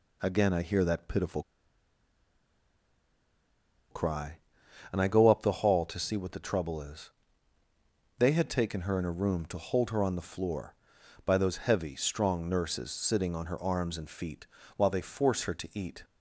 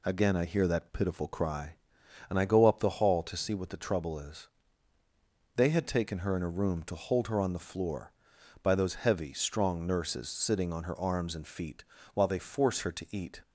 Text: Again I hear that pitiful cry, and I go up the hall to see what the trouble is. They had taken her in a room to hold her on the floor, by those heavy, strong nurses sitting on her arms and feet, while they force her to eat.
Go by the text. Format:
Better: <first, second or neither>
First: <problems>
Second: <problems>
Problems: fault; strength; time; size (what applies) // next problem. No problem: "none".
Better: second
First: pauses between "pitiful" and "cry"; strong; at 1.4 s; 2.5 s long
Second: none